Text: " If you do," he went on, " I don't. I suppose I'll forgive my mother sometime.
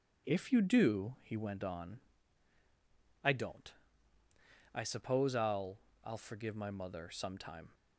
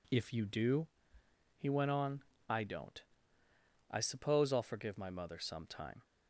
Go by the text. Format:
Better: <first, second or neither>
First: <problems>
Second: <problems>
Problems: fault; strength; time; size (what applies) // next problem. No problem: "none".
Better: second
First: says "I'll" twice; at 6.0 s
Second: none